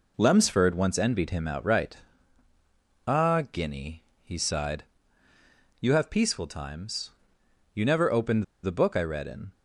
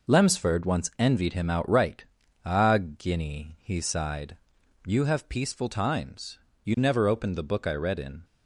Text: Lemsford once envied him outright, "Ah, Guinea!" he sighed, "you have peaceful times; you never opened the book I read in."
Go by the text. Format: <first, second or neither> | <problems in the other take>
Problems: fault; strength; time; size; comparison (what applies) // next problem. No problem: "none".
second | pauses between "opened" and "the"; slight; at 8.4 s; 0.19 s long